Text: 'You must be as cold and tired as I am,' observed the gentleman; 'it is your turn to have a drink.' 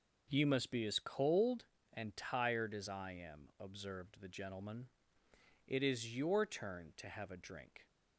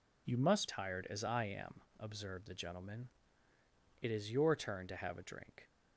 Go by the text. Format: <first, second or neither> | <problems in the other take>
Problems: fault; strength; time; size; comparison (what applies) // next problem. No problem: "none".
first | skips "be as cold and"; at 0.6 s